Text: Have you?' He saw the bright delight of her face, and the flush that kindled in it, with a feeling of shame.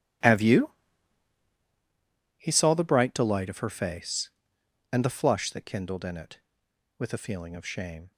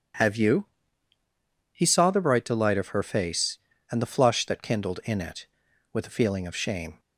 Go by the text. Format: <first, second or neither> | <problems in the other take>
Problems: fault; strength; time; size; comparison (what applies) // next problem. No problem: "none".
second | gets quieter; strong; throughout; 17.5 dB